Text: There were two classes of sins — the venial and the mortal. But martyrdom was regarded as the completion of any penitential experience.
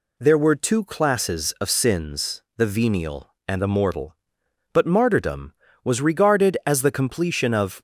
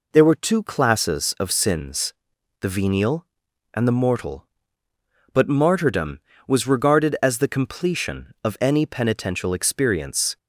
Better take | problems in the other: second | stops before "any penitential experience"; at 7.7 s

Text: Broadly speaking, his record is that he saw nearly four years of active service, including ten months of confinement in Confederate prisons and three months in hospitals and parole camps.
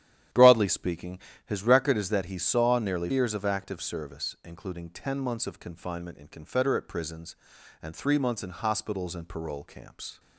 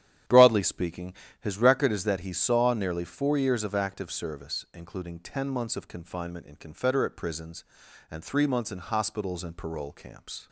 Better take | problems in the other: second | starts louder than the rest; strong; until 1.5 s; 11 dB; strong in the second // skips "four"; at 3.1 s

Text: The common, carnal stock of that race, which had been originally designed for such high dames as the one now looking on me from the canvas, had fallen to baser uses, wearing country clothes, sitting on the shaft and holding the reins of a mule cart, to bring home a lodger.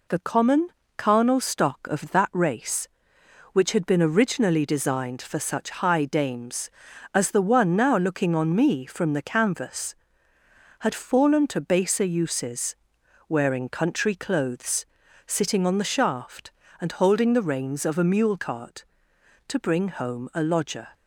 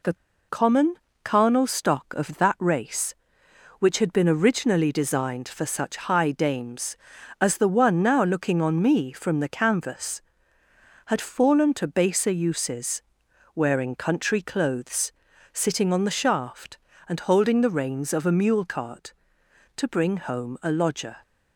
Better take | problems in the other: first | pauses between "The" and "common"; slight; at 0.1 s; 0.34 s long

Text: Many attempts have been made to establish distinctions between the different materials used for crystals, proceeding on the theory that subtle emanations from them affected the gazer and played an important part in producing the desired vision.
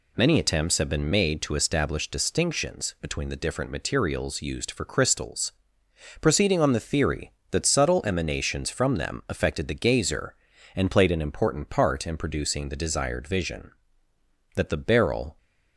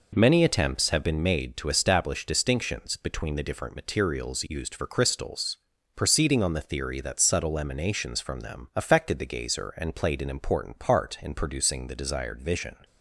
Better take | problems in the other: second | goes on to say "That the beryl"; noticeable; from 14.5 s on; 0.82 s long

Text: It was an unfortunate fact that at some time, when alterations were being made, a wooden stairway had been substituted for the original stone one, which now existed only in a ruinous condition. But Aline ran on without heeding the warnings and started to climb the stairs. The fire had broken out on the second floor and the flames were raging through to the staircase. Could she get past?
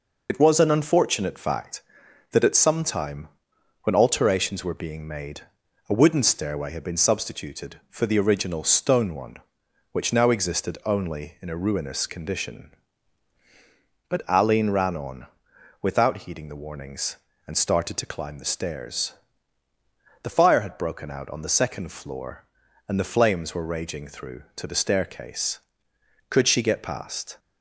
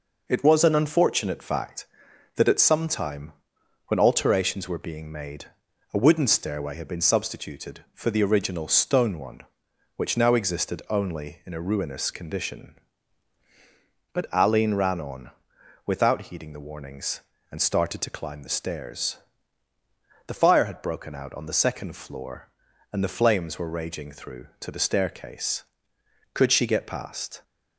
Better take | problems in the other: second | loses the start of "It"; at 0.2 s; 55 ms // pauses between "on" and "without"; noticeable; at 15.2 s; 0.54 s long; noticeable in the second

